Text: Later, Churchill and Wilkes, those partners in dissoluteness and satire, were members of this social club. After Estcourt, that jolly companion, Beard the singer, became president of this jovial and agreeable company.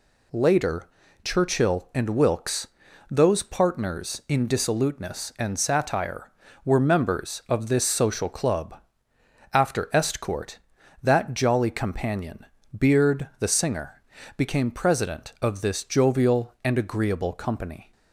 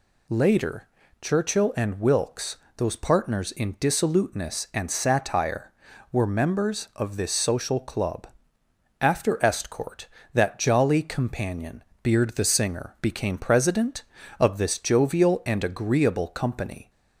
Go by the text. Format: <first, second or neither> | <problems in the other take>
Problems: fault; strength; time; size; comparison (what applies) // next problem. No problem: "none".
neither | none